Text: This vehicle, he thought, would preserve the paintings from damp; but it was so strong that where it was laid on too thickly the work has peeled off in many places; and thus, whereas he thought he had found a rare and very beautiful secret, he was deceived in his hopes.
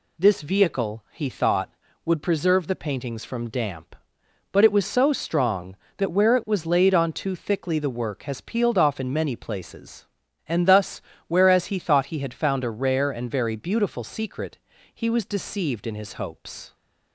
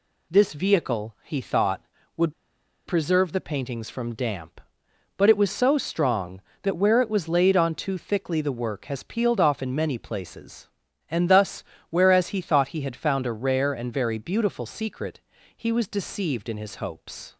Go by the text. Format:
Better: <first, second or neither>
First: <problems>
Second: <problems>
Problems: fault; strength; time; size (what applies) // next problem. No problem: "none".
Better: first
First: none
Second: pauses between "would" and "preserve"; noticeable; at 2.3 s; 0.53 s long